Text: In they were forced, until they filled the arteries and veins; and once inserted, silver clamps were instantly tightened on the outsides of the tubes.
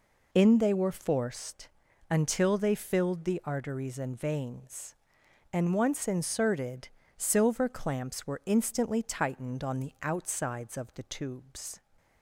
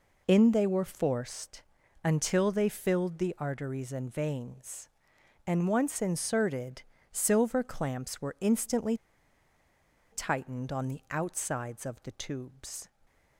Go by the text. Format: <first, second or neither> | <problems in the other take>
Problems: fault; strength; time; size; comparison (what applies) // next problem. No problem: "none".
first | pauses between "instantly" and "tightened"; at 8.9 s; 1.1 s long